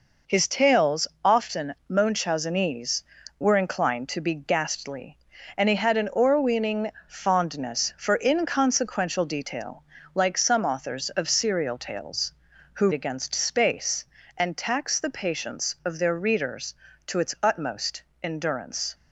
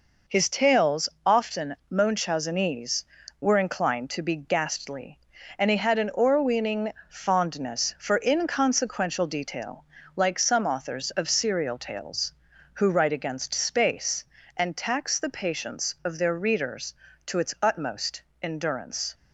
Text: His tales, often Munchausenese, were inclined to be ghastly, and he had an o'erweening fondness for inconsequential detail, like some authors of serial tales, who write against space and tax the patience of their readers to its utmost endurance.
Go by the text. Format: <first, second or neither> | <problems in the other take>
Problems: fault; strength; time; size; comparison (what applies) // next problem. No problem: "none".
second | pauses between "o'erweening" and "fondness"; slight; at 6.8 s; 0.18 s long; slight in the second // skips "write"; at 12.9 s // pauses between "utmost" and "endurance"; slight; at 18.0 s; 0.18 s long; slight in the second